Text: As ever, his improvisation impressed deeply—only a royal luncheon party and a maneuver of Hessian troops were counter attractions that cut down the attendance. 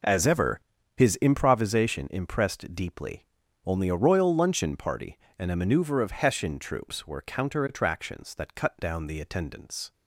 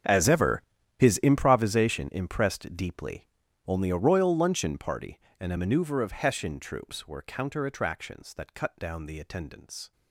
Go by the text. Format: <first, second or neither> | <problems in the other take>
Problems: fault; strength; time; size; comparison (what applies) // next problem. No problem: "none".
first | gets quieter; strong; throughout; 19 dB